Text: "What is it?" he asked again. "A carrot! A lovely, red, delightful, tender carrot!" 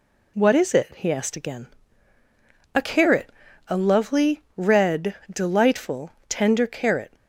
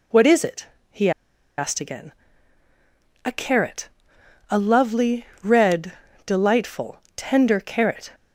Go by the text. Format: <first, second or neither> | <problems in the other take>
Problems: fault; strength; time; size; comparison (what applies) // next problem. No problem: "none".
first | pauses between "he" and "asked"; noticeable; at 1.1 s; 0.47 s long